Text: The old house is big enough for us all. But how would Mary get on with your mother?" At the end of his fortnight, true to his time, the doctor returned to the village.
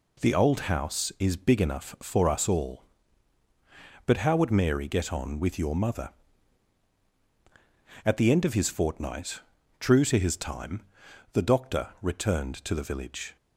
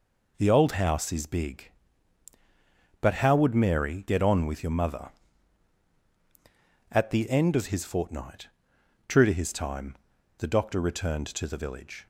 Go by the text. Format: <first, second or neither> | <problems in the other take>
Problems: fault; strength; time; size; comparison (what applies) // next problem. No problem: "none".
first | skips "enough for us all"; at 2.3 s